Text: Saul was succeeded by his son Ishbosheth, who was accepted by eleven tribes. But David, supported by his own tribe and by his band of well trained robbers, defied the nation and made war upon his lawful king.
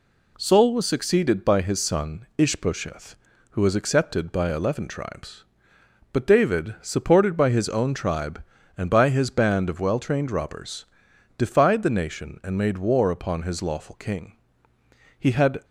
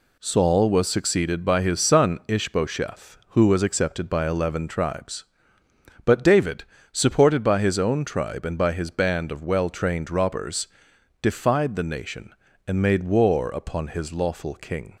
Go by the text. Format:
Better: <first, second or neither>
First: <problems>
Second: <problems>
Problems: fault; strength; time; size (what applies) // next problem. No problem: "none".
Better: second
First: goes on to say "He had"; slight; from 15.1 s on; 0.46 s long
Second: none